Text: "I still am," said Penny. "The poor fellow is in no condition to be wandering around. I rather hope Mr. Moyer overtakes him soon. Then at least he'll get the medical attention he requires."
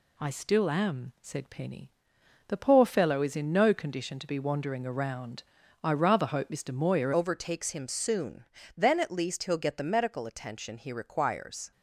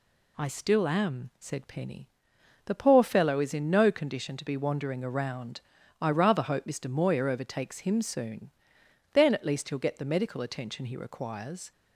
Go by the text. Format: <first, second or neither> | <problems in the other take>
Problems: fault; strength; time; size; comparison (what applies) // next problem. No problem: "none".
second | changes voice at "overtakes"; from 7.1 s on; 4.6 s long